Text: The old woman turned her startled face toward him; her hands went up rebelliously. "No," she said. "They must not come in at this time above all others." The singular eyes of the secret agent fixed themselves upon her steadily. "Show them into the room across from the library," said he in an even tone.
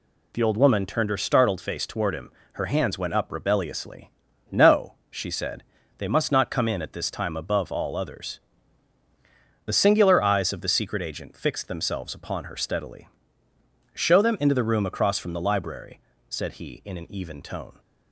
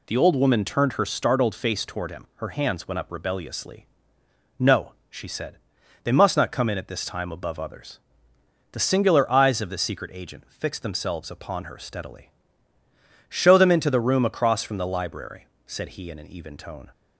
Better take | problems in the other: first | skips "all"; at 7.5 s

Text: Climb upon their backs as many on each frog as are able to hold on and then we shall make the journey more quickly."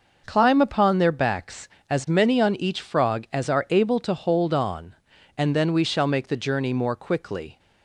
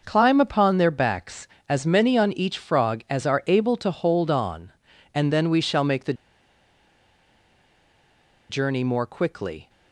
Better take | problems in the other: first | pauses between "the" and "journey"; strong; at 6.1 s; 2.3 s long

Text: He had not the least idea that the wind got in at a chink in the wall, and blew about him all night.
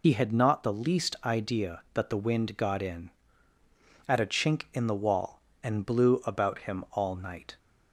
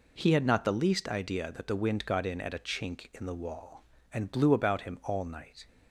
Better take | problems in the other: second | loses the start of "He"; at 0.0 s; 90 ms

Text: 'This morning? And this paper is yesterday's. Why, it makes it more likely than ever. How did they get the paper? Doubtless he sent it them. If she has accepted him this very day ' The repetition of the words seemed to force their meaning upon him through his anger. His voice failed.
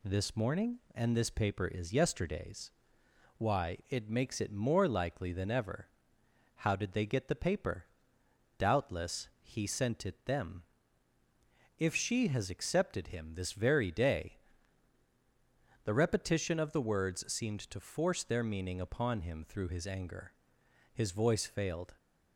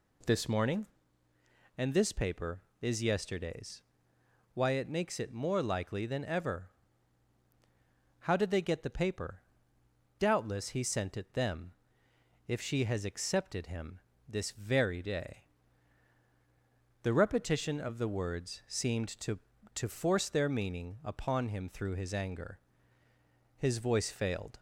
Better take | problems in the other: first | pauses between "him" and "this"; slight; at 13.9 s; 0.28 s long // says "to" twice; at 19.7 s

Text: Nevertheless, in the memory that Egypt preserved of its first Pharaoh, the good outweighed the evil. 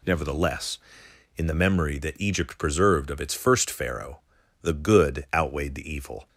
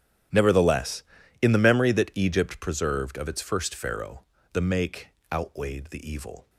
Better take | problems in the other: first | starts louder than the rest; strong; until 1.7 s; 11.5 dB // says "make" for "good"; at 4.6 s

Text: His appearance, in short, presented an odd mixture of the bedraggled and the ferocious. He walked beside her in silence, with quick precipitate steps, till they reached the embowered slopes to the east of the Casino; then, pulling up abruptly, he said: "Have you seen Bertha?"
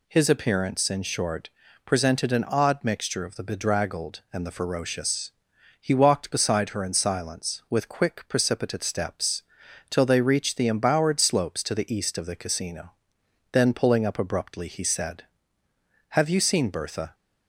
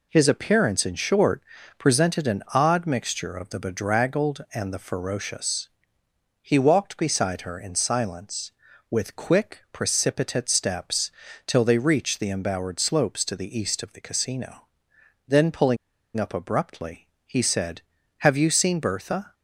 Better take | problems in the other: first | pauses between "pulling" and "up"; at 15.7 s; 0.40 s long

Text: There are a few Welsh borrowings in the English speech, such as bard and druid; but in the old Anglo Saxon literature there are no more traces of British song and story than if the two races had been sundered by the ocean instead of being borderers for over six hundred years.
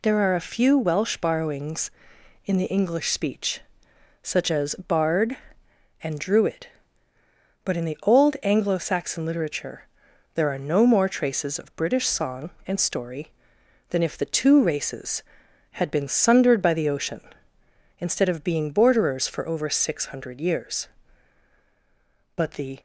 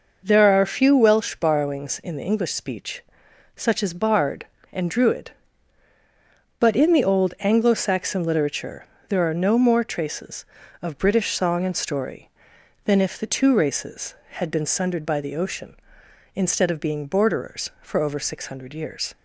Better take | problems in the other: second | pauses between "literature" and "there"; noticeable; at 9.8 s; 0.48 s long; slight in the second // goes on to say "But the"; slight; from 22.3 s on; 0.44 s long

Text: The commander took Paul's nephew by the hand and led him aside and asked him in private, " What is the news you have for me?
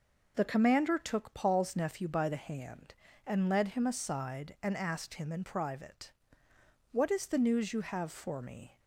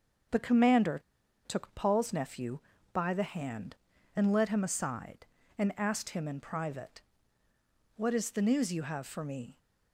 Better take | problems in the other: first | starts louder than the rest; until 1.7 s; 6.5 dB // pauses between "commander" and "took"; noticeable; at 0.9 s; 0.46 s long

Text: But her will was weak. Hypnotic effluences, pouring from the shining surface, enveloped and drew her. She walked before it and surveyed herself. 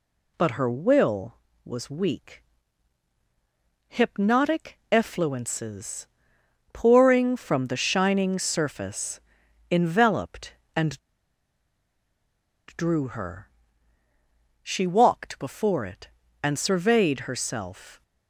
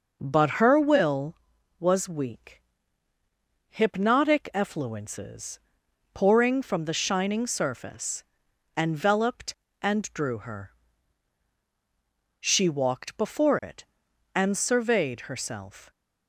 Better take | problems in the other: second | pauses between "and" and "drew"; strong; at 10.9 s; 1.7 s long

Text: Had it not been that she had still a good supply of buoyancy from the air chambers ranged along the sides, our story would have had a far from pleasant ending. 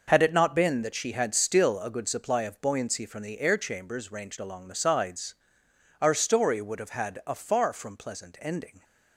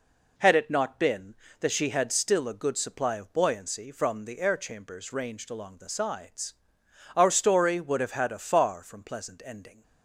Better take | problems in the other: neither | none

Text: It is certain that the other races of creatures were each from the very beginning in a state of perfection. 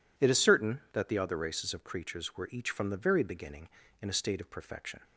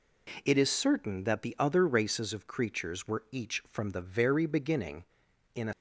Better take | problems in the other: first | stops before "state of perfection"; at 5.7 s

